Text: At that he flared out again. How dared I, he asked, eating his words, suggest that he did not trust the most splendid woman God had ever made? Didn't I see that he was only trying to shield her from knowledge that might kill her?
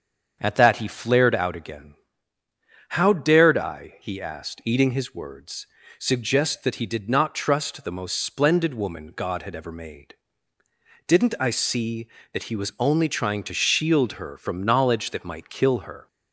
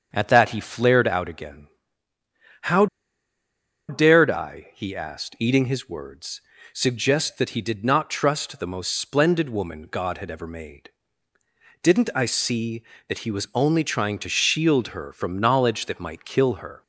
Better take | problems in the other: first | starts louder than the rest; until 1.1 s; 7 dB; also in the first // pauses between "How" and "dared"; at 2.8 s; 1.0 s long

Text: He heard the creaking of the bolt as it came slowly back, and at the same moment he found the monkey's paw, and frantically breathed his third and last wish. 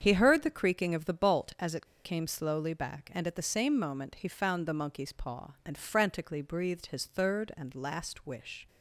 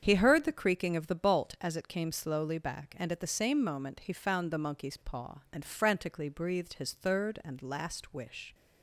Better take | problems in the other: second | starts louder than the rest; strong; until 1.0 s; 7.5 dB; strong in the second // pauses between "it" and "came"; slight; at 1.8 s; 0.18 s long

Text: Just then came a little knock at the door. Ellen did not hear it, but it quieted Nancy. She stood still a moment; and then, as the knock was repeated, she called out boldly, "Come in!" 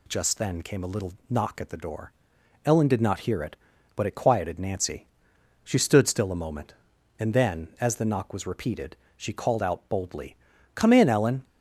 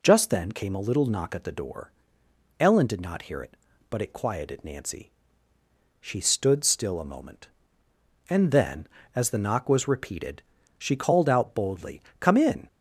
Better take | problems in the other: second | pauses between "little" and "knock"; slight; at 1.1 s; 0.16 s long // goes on to say "Ellen"; slight; from 11.0 s on; 0.36 s long

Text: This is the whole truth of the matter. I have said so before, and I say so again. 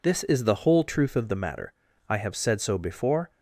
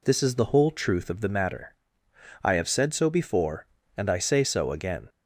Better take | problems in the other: second | stops before "and I say so again"; at 3.3 s

